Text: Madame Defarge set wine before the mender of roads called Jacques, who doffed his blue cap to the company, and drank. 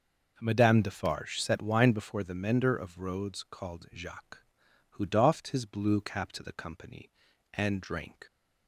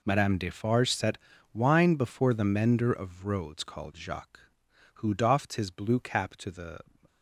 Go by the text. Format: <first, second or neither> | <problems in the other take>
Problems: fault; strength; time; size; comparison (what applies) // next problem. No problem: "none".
first | pauses between "set" and "wine"; at 1.1 s; 0.38 s long // stops before "company and drank"; at 7.0 s